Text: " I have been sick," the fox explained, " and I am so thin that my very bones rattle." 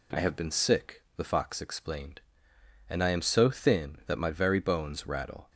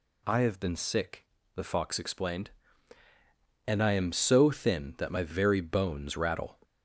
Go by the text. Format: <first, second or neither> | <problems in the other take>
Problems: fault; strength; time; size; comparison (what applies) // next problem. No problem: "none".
first | gets louder; throughout; 4 dB